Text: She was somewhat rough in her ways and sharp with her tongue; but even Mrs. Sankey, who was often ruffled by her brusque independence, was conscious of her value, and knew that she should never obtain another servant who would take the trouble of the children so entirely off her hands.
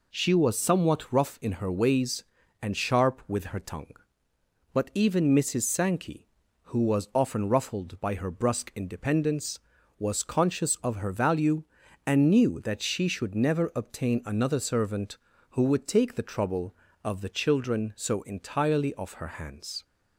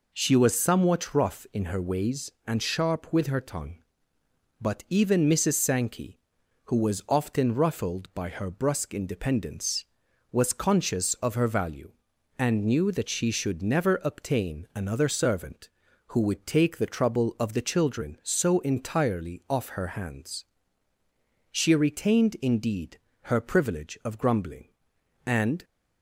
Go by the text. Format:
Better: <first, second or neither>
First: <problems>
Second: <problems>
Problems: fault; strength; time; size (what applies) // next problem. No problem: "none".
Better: first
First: none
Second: goes on to say "She retained indeed her privilege of grumbling and"; strong; from 21.5 s on; 4.1 s long